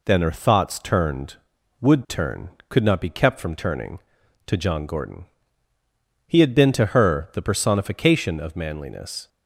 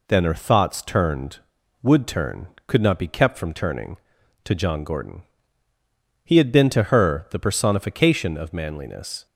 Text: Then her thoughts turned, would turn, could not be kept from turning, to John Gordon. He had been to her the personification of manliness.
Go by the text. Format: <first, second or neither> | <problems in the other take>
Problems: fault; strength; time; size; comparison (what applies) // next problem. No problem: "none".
neither | none